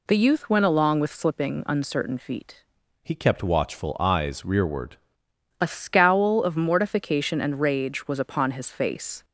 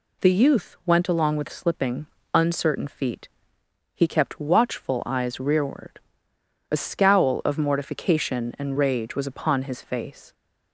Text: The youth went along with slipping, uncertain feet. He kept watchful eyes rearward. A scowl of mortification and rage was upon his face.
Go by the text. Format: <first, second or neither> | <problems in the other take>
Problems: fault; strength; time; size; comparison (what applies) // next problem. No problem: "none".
second | changes voice from "He" to "rearward"; from 3.0 to 4.9 s; 1.9 s long